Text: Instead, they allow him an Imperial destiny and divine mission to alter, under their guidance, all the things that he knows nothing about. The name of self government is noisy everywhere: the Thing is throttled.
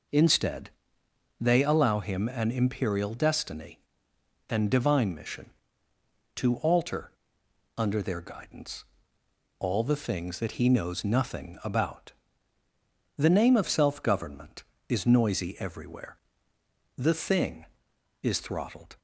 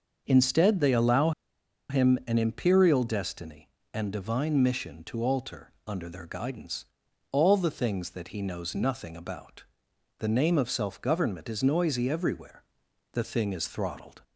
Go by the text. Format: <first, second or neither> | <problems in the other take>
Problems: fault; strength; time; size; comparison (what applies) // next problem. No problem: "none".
first | starts louder than the rest; until 1.2 s; 6.5 dB // pauses between "allow" and "him"; noticeable; at 1.3 s; 0.58 s long